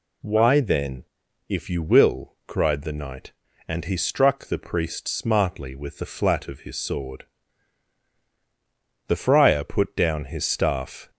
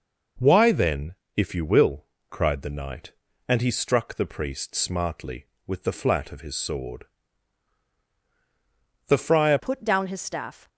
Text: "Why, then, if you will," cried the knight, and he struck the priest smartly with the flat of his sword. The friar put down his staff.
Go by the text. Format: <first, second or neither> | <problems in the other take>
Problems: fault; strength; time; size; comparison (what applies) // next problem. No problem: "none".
first | changes voice at "put"; from 9.5 s on; 1.1 s long